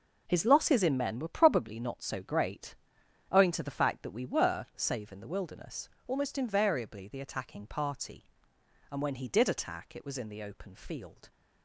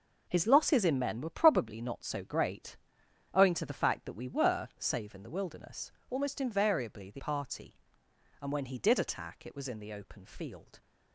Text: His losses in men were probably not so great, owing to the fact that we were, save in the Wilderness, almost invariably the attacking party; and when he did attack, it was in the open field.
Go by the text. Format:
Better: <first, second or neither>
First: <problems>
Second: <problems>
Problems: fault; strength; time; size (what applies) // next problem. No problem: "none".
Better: first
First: none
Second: skips "attacking"; at 7.1 s